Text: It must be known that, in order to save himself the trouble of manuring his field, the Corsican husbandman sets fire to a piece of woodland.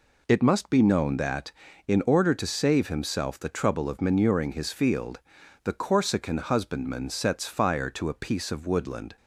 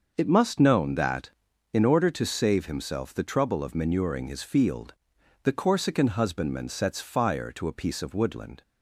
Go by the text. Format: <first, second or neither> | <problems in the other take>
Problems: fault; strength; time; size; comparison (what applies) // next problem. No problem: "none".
first | starts louder than the rest; until 1.1 s; 6 dB // skips "be"; at 0.5 s